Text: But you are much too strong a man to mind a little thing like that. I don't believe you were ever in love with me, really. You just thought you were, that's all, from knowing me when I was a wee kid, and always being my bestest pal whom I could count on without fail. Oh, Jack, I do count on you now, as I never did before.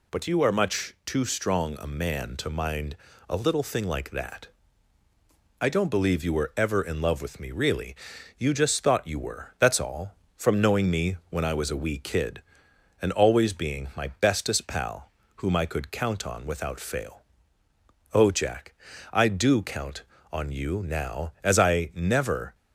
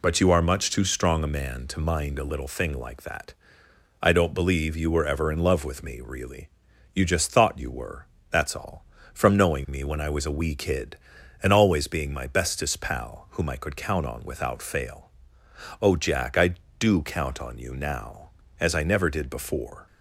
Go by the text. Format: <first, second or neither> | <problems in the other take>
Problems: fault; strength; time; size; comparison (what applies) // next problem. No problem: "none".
second | pauses between "mind" and "a"; slight; at 2.9 s; 0.32 s long // pauses between "pal" and "whom"; slight; at 15.0 s; 0.28 s long // stops before "did before"; at 22.5 s